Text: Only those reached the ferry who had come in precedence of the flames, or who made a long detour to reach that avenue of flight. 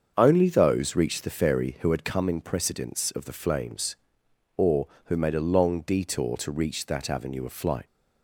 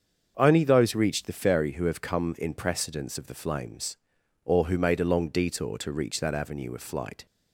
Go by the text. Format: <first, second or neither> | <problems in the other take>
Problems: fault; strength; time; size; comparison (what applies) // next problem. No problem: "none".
first | starts louder than the rest; until 1.3 s; 7 dB; also in the first // says "have" for "had"; at 1.8 s